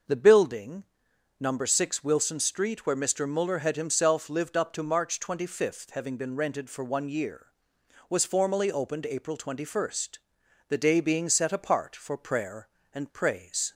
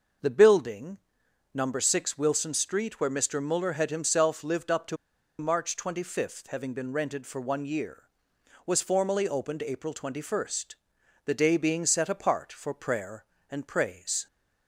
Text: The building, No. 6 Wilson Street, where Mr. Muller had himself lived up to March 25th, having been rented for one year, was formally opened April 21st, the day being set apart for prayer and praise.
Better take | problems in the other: first | pauses between "to" and "March"; at 4.9 s; 0.44 s long

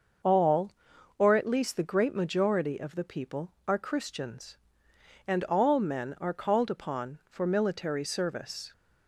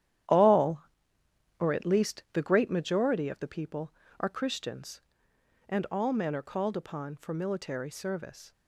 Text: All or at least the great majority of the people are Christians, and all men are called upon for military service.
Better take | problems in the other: first | gets quieter; strong; throughout; 10 dB // starts louder than the rest; strong; until 2.0 s; 11 dB; also in the first

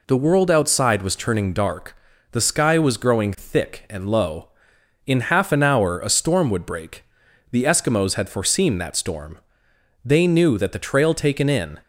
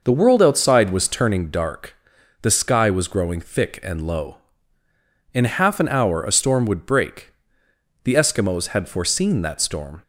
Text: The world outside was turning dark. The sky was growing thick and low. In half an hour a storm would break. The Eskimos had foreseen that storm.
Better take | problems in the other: second | goes on to say "They knew that the trail taken in"; strong; from 10.0 s on; 1.7 s long

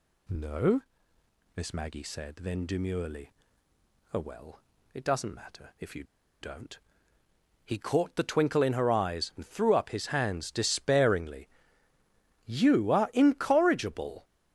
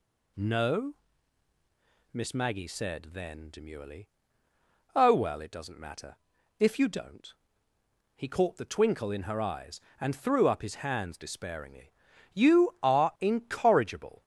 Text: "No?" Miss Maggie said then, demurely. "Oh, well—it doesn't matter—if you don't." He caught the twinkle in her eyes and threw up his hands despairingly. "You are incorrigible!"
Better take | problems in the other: second | pauses between "you" and "don't"; at 6.0 s; 0.38 s long

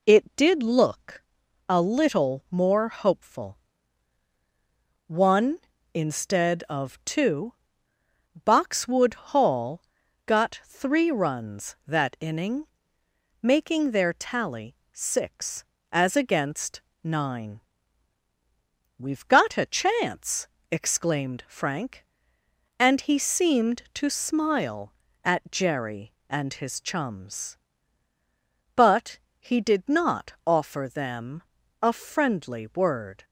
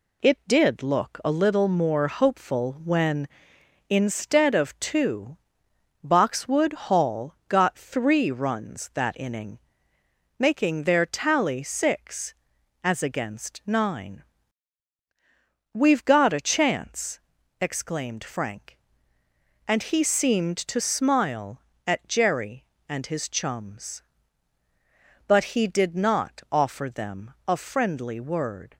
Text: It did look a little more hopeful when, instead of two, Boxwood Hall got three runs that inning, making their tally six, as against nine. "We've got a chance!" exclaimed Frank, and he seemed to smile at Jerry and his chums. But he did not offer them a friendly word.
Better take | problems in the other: second | pauses between "look" and "a"; noticeable; at 1.2 s; 0.46 s long // says "one" for "when"; at 5.0 s // pauses between "Hall" and "got"; at 9.8 s; 0.42 s long // pauses between "tally" and "six"; slight; at 14.7 s; 0.20 s long // pauses between "against" and "nine"; slight; at 16.8 s; 0.22 s long // pauses between "But" and "he"; slight; at 29.1 s; 0.20 s long // pauses between "them" and "a"; at 31.4 s; 0.39 s long; slight in the second

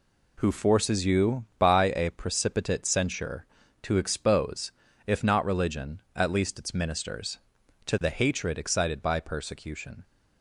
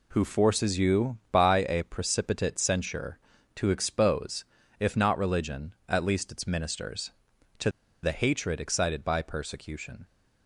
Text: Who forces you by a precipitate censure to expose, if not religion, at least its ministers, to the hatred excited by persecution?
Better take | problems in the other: first | pauses between "to" and "the"; slight; at 7.6 s; 0.33 s long

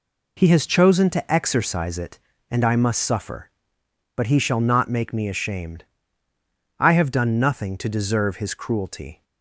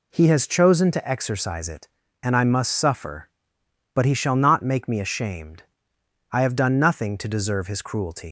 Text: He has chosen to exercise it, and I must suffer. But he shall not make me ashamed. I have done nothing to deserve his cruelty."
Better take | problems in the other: first | leaves "cruelty" unfinished; at 8.2 s; 135 ms

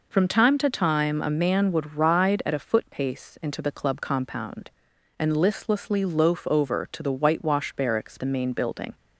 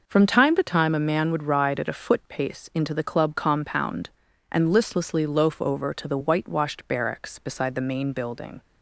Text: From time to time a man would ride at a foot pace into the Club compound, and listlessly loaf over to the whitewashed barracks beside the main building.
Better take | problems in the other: second | skips "beside"; at 8.1 s

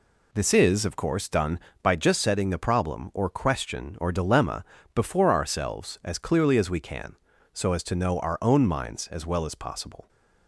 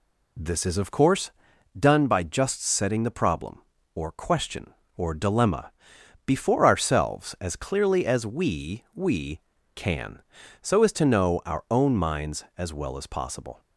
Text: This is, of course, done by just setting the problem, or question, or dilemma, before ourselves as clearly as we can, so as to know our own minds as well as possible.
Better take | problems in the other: first | says "we" twice; at 8.9 s

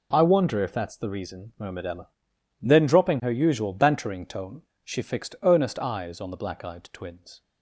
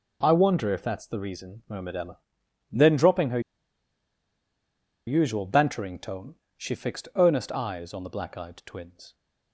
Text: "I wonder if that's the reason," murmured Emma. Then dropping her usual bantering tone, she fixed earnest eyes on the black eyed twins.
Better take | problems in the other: first | pauses between "her" and "usual"; strong; at 3.3 s; 1.6 s long

